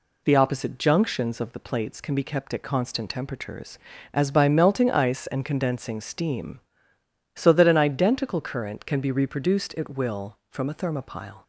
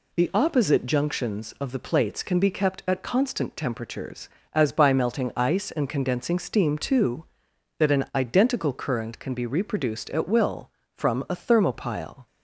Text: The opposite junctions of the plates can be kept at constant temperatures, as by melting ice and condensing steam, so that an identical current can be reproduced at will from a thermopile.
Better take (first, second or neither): first